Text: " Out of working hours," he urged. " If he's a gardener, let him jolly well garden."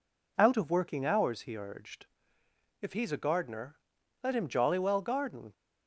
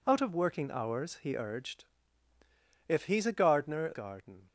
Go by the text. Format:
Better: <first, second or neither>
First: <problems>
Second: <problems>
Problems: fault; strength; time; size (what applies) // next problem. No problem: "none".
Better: first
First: none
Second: skips "let him jolly well"; at 3.9 s